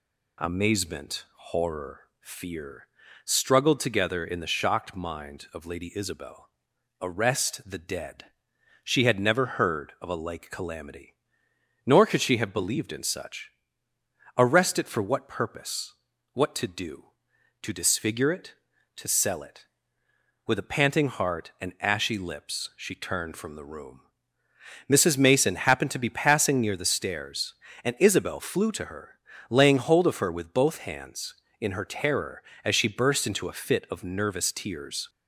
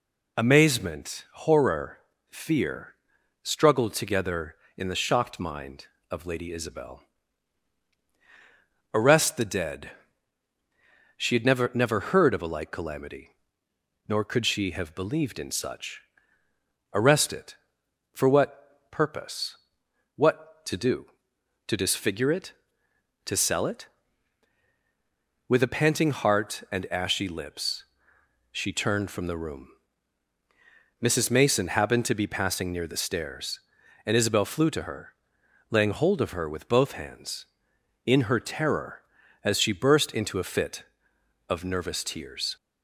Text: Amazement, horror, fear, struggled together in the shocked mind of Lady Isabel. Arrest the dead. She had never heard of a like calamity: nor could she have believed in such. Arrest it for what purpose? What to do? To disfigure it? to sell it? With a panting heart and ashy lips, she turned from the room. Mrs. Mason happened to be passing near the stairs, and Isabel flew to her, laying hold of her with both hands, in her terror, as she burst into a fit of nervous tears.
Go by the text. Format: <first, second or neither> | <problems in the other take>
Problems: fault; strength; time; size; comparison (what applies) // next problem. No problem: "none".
first | says "never" twice; at 11.7 s